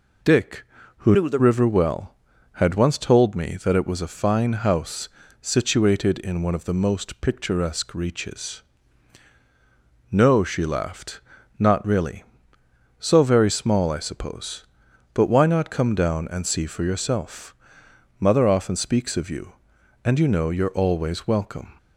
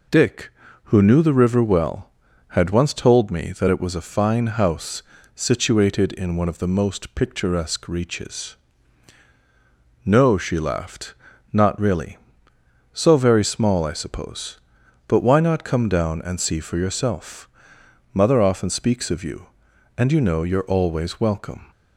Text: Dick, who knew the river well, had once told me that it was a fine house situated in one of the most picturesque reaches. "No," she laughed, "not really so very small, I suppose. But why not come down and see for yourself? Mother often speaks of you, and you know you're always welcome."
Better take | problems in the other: second | changes voice from "knew" to "the"; from 1.1 to 1.3 s; 0.2 s long // pauses between "house" and "situated"; slight; at 5.0 s; 0.32 s long; slight in the second

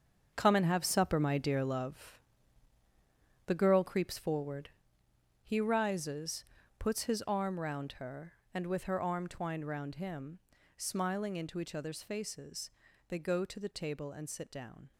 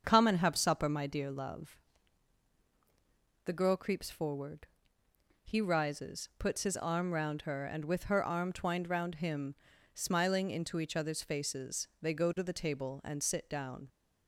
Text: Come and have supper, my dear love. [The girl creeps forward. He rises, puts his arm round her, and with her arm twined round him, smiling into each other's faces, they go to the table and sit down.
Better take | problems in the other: second | gets quieter; strong; throughout; 10 dB // starts louder than the rest; until 1.3 s; 7 dB; also in the second

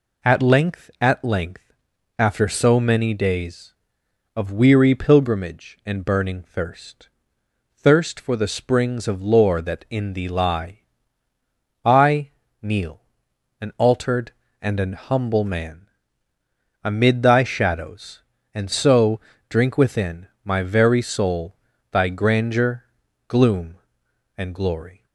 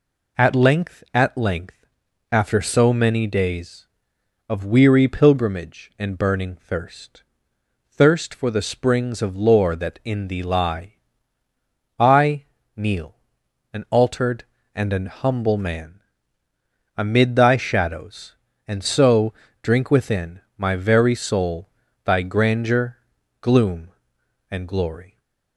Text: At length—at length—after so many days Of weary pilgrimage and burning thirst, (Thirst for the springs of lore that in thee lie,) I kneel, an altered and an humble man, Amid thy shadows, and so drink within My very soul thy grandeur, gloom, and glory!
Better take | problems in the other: neither | pauses between "I" and "kneel"; slight; the same in both // pauses between "so" and "drink"; slight; the same in both // pauses between "within" and "My"; slight; the same in both // pauses between "soul" and "thy"; slight; the same in both

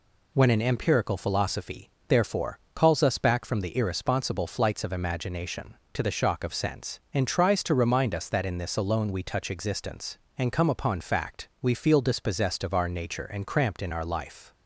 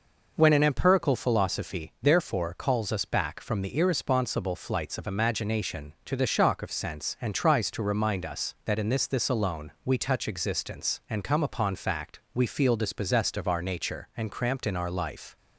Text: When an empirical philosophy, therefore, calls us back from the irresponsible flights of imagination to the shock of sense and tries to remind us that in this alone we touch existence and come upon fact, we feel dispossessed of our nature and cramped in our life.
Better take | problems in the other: first | says "this" twice; at 9.0 s

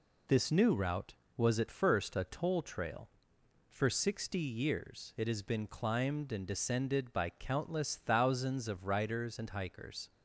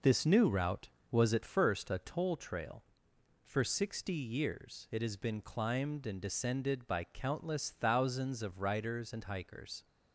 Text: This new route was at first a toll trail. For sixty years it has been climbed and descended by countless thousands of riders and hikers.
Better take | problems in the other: first | starts louder than the rest; noticeable; until 1.7 s; 5 dB

